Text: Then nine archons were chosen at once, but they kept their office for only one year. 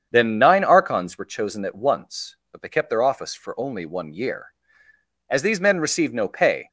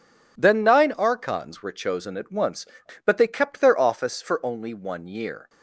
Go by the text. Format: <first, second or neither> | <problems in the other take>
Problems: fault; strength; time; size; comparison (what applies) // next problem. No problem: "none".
second | starts louder than the rest; strong; until 1.1 s; 7.5 dB // goes on to say "As these men received no pay"; from 5.2 s on; 1.4 s long